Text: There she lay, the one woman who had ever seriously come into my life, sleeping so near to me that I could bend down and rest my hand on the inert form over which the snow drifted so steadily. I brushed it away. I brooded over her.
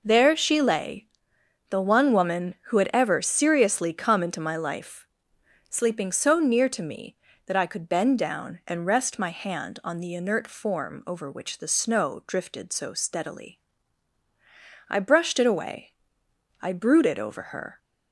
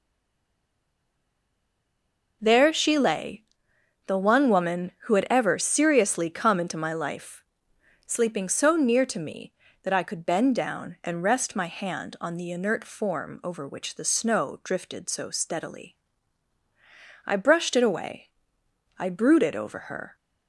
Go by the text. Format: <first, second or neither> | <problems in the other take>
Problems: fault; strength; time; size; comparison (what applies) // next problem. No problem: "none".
first | stays silent before the first word; until 2.4 s; 2.4 s long